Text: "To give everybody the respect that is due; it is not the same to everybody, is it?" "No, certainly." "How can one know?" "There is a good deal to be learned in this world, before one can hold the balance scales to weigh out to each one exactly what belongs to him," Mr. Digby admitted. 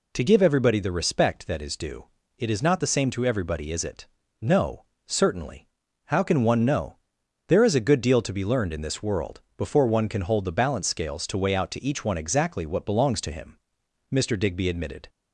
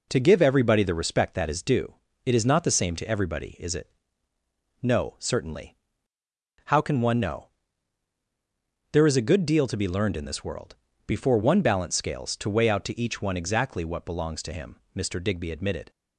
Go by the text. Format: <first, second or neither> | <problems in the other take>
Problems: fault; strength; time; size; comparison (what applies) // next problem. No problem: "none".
first | skips "can hold the"; at 11.6 s